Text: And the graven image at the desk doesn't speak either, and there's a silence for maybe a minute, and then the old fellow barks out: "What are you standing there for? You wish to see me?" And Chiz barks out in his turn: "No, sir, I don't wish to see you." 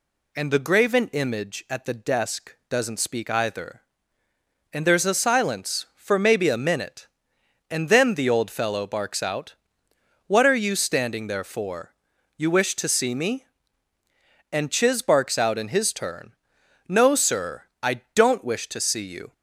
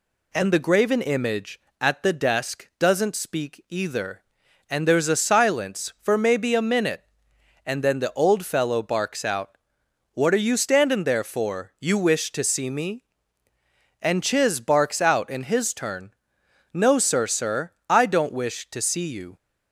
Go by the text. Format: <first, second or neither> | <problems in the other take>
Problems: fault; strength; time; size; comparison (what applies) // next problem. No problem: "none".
first | says "sir" twice; at 17.2 s